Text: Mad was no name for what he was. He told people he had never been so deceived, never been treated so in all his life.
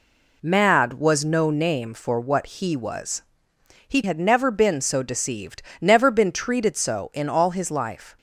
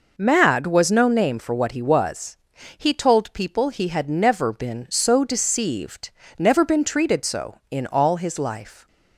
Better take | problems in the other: second | skips "told people he"; at 4.0 s

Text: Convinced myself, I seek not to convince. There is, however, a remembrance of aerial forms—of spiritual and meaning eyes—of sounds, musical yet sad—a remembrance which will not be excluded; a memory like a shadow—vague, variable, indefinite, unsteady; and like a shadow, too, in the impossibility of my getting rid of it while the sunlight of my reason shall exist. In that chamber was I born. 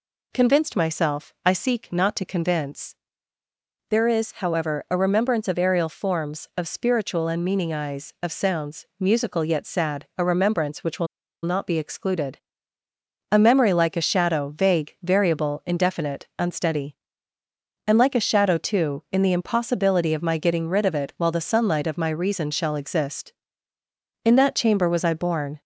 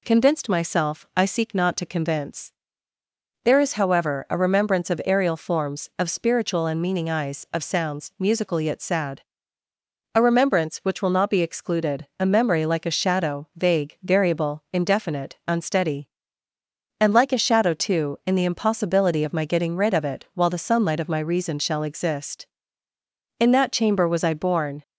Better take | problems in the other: second | pauses between "will" and "not"; at 11.0 s; 0.37 s long

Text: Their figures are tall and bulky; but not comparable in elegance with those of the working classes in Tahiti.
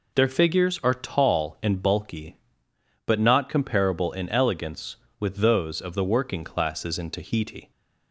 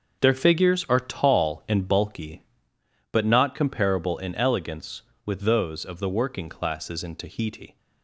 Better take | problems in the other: first | gets quieter; strong; throughout; 11 dB

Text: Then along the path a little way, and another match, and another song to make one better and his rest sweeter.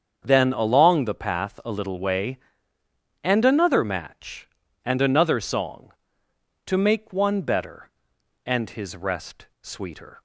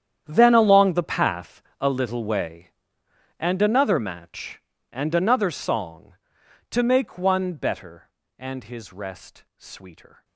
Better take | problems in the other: first | gets quieter; strong; throughout; 18.5 dB // starts louder than the rest; strong; until 1.2 s; 9.5 dB; strong in the first // pauses between "path" and "a"; slight; at 1.6 s; 0.20 s long

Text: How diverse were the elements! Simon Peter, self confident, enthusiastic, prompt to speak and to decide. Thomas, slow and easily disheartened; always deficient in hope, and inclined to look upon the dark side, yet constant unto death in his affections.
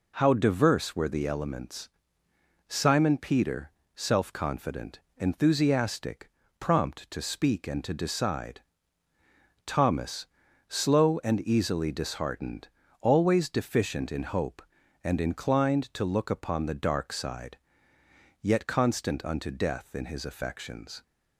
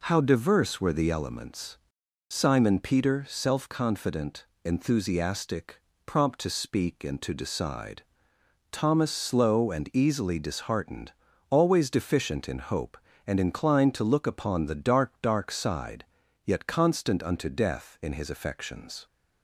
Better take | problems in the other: first | says "dark" twice; at 15.2 s

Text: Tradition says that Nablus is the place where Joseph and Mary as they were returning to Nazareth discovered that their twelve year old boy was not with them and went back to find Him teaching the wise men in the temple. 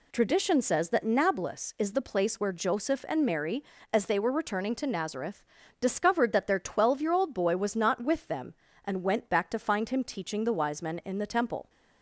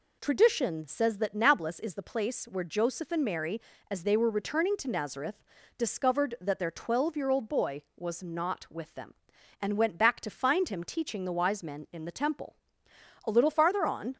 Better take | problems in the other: first | pauses between "Nazareth" and "discovered"; slight; at 5.4 s; 0.34 s long; slight in the first // goes on to say "A little farther on"; noticeable; from 13.2 s on; 0.90 s long

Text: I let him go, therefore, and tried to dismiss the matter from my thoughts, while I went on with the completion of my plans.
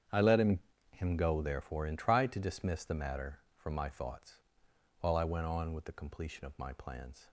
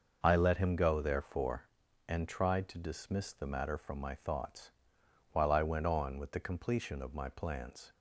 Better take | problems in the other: second | starts louder than the rest; strong; until 1.4 s; 8.5 dB; also in the second // says "him" twice; at 0.9 s

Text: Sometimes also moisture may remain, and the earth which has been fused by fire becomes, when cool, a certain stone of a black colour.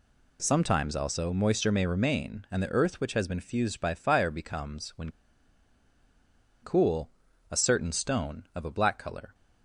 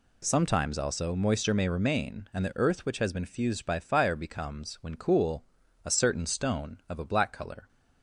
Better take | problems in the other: second | pauses between "when" and "cool"; strong; at 5.1 s; 1.5 s long

